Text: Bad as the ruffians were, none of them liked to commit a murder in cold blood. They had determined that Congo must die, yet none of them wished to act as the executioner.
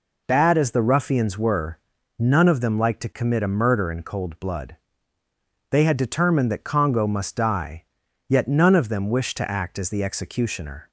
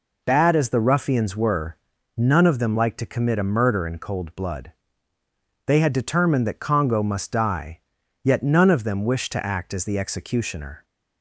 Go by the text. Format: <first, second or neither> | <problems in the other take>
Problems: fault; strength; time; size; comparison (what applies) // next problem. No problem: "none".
neither | none